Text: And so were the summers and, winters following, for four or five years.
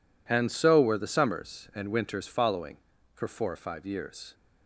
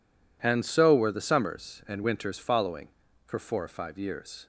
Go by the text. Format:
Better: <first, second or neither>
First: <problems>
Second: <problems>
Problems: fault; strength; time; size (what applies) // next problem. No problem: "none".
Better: neither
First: none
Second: none